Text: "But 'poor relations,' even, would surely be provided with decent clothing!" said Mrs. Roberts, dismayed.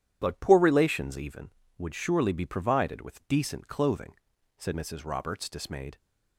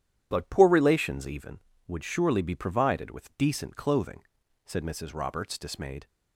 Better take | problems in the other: neither | starts louder than the rest; strong; the same in both

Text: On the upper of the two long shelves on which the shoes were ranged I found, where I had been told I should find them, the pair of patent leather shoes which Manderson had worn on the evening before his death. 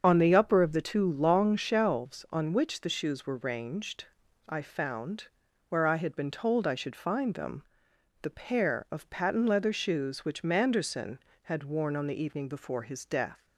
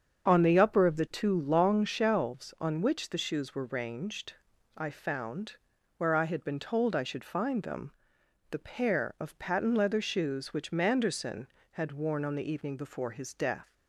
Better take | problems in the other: second | loses the start of "On"; at 0.0 s; 25 ms // starts louder than the rest; until 1.0 s; 7 dB; also in the second // pauses between "ranged" and "I"; at 4.0 s; 0.42 s long; also in the second

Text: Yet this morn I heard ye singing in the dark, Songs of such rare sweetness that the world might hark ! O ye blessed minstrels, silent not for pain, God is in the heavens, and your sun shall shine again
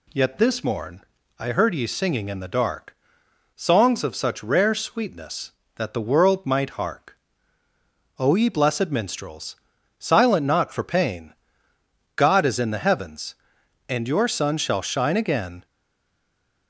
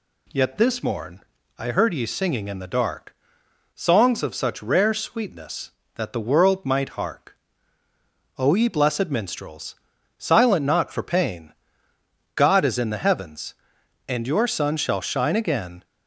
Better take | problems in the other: second | pauses between "morn" and "I"; slight; at 1.0 s; 0.36 s long; slight in the second // stays silent after the last word; from 15.6 s on; 1.0 s long

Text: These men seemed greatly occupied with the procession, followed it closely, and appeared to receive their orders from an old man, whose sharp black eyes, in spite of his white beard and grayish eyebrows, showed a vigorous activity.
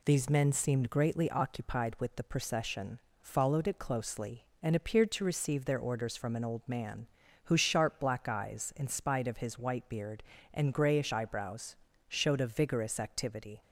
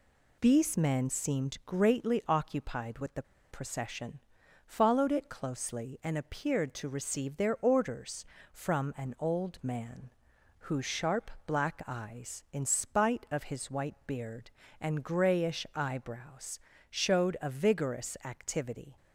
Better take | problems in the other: first | pauses between "the" and "procession"; slight; at 3.2 s; 0.28 s long

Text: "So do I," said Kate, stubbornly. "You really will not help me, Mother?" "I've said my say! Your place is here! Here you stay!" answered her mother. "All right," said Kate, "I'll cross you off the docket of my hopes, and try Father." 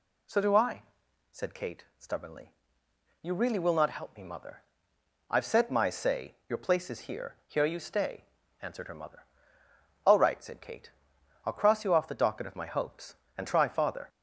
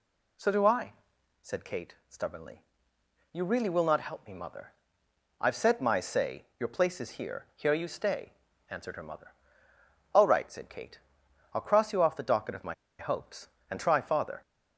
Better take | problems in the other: first | pauses between "my" and "hopes"; slight; at 12.7 s; 0.26 s long

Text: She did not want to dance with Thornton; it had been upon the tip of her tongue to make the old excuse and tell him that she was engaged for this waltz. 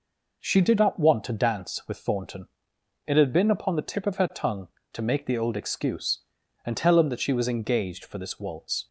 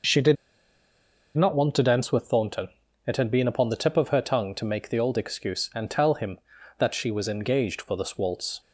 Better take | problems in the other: first | pauses between "did" and "not"; at 0.3 s; 1.0 s long

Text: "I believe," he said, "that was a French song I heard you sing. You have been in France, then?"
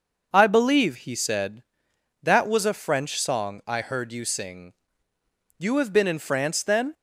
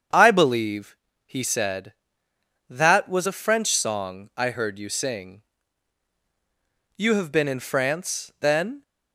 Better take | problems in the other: neither | starts louder than the rest; the same in both

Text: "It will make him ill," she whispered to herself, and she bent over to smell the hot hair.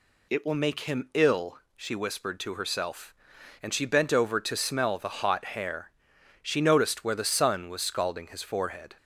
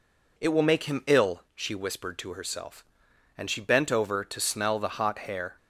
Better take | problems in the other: second | goes on to say "She noticed where the sun was scalding his forehead"; strong; from 6.4 s on; 2.5 s long

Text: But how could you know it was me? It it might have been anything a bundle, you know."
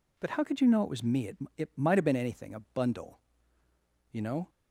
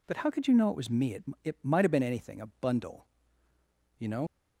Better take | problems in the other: first | pauses between "It" and "it"; slight; at 1.2 s; 0.20 s long; slight in the first // pauses between "a" and "bundle"; slight; at 2.4 s; 0.16 s long; slight in the first // leaves "know" unfinished; at 4.2 s; 90 ms

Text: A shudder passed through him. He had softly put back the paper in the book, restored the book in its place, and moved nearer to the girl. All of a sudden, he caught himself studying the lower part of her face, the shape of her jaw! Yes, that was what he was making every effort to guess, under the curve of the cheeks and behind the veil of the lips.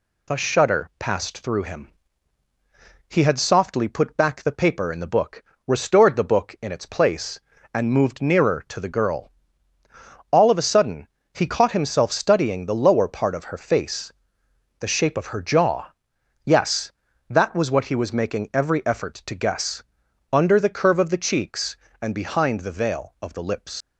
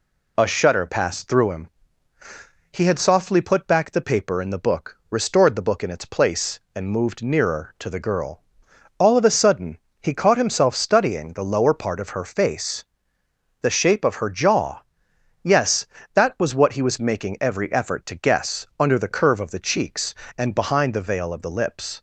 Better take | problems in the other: second | leaves "lips" unfinished; at 23.8 s; 80 ms

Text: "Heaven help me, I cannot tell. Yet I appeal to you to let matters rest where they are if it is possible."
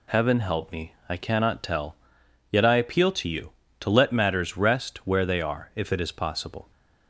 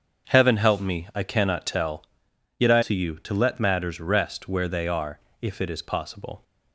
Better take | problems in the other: first | starts louder than the rest; until 1.3 s; 7 dB // skips "appeal"; at 2.8 s // pauses between "are" and "if"; slight; at 5.1 s; 0.22 s long

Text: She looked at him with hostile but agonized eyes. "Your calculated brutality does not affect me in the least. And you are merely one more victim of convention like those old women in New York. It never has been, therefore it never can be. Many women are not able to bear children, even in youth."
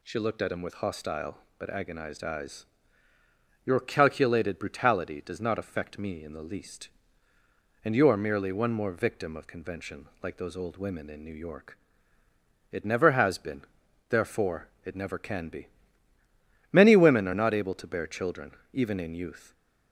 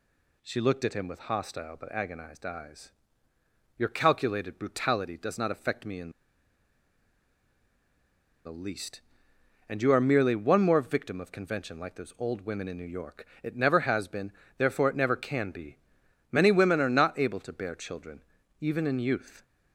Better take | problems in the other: first | pauses between "in" and "the"; strong; at 6.1 s; 2.3 s long

